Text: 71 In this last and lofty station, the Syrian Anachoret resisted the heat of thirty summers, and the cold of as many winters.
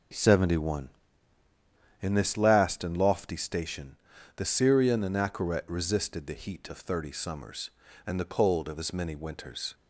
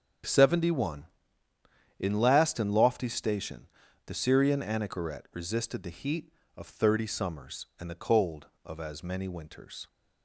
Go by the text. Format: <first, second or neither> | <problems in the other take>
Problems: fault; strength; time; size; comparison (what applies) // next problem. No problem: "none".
first | starts louder than the rest; until 2.1 s; 6.5 dB // skips "this"; at 2.1 s